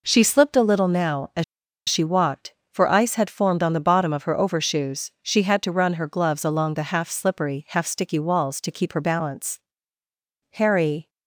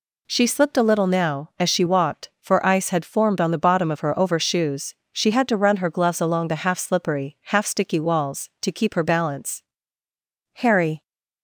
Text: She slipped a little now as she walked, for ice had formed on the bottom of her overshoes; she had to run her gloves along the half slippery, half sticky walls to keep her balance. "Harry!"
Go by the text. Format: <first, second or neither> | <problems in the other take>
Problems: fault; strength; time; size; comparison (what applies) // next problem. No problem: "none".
second | pauses between "as" and "she"; at 1.4 s; 0.44 s long